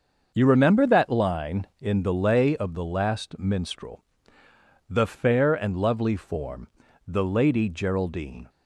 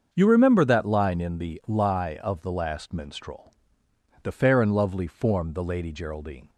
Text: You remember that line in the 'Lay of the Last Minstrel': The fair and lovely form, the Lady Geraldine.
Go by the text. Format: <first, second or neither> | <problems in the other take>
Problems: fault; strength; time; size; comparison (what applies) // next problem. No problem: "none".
first | starts louder than the rest; until 1.1 s; 6.5 dB; also in the first // says "Lie" for "Lay"; at 1.6 s